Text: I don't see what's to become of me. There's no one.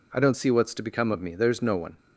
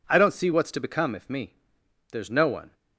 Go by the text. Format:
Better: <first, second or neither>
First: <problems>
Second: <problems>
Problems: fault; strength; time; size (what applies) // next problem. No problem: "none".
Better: first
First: none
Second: says "if" for "of"; at 1.1 s